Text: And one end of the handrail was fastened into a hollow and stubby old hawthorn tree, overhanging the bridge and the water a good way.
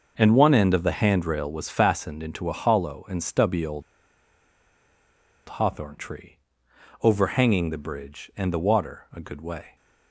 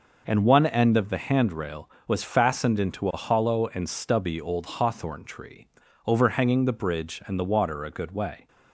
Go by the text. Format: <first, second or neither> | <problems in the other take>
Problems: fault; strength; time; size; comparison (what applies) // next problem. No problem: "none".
second | starts louder than the rest; noticeable; until 1.1 s; 6 dB // pauses between "old" and "hawthorn"; strong; at 3.8 s; 1.6 s long